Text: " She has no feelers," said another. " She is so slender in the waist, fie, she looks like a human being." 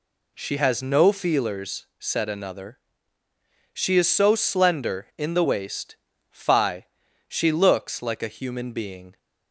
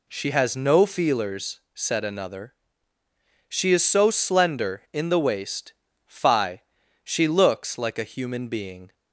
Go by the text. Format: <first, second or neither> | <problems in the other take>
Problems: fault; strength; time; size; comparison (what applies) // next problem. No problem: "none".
neither | none